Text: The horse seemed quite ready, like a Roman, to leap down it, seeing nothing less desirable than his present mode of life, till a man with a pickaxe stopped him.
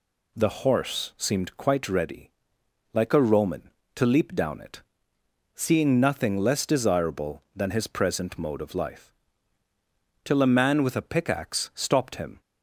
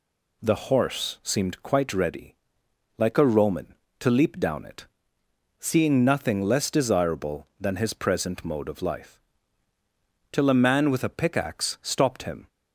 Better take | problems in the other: neither | none

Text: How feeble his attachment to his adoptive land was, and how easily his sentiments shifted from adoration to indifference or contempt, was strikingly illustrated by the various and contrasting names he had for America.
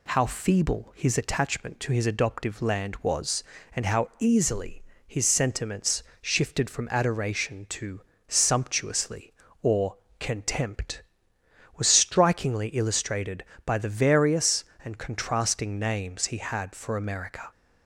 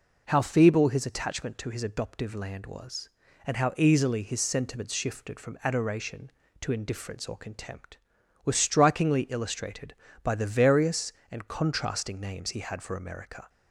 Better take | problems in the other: second | pauses between "easily" and "his"; slight; at 4.8 s; 0.24 s long // pauses between "sentiments" and "shifted"; slight; at 6.0 s; 0.20 s long // says "sumptuously" for "indifference"; at 8.2 s // pauses between "or" and "contempt"; slight; at 9.9 s; 0.24 s long

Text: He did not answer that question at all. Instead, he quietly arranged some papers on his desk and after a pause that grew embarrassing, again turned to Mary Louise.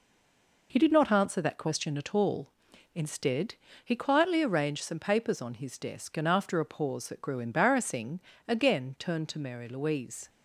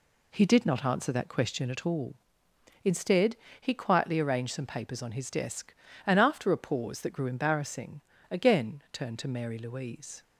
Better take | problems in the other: second | stays silent before the first word; slight; until 0.7 s; 0.7 s long

